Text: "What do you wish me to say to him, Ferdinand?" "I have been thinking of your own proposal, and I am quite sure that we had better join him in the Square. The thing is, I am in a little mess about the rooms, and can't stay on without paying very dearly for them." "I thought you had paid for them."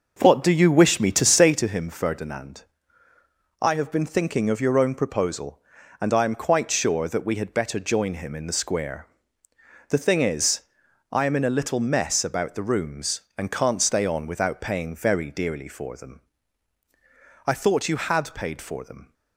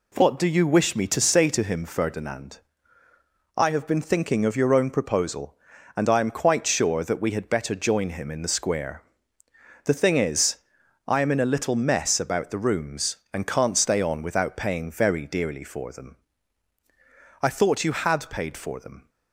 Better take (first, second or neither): second